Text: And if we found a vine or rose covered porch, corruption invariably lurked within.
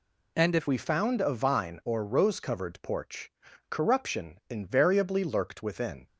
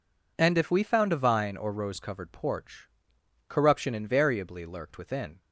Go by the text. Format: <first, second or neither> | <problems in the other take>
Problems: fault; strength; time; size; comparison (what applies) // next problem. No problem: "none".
second | changes voice at "we"; from 0.6 s on; 5.4 s long